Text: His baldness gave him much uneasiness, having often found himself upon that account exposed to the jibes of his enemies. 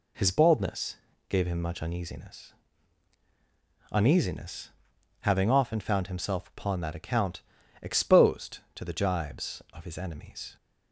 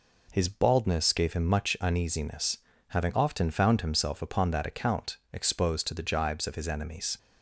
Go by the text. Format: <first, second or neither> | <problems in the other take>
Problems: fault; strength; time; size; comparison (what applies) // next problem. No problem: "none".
second | pauses between "baldness" and "gave"; slight; at 0.9 s; 0.32 s long // says "uneasiness" twice; at 3.9 s // pauses between "account" and "exposed"; at 7.4 s; 0.40 s long; slight in the second